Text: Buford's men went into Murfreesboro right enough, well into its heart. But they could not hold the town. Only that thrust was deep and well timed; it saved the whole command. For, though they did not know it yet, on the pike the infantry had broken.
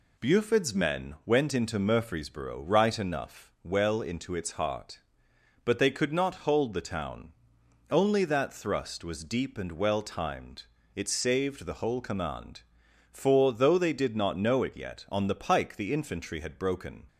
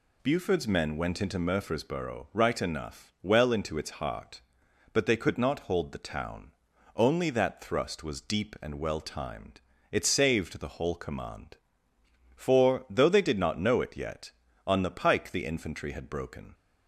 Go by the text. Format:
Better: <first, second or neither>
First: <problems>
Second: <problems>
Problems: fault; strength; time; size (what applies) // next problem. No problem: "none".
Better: neither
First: none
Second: none